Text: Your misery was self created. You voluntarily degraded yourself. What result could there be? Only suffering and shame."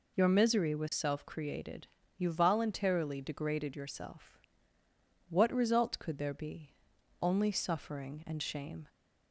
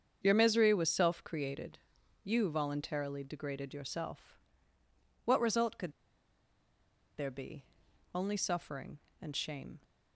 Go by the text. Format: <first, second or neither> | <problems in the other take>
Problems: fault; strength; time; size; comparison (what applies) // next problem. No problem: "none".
first | starts louder than the rest; strong; until 1.2 s; 7 dB // pauses between "could" and "there"; strong; at 5.9 s; 1.2 s long